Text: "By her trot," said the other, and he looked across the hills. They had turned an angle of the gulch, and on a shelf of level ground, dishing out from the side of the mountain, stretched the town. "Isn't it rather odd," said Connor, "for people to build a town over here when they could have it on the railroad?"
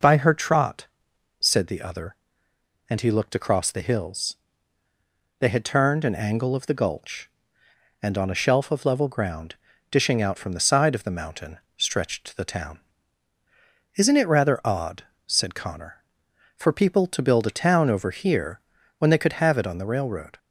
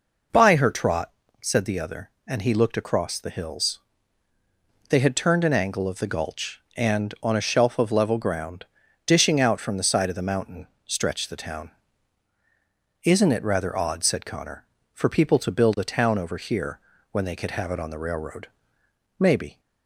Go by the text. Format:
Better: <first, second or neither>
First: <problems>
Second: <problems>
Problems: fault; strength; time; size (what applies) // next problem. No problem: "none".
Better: first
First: pauses between "here" and "when"; at 18.5 s; 0.40 s long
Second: pauses between "here" and "when"; slight; at 16.7 s; 0.32 s long // goes on to say "Maybe"; slight; from 19.1 s on; 0.40 s long